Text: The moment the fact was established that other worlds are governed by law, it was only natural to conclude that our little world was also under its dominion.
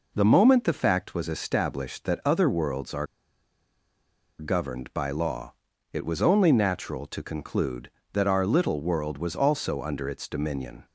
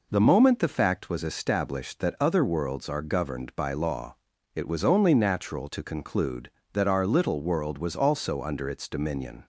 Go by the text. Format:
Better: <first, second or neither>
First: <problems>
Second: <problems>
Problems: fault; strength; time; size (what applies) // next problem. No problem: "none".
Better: second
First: pauses between "are" and "governed"; strong; at 3.0 s; 1.3 s long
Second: none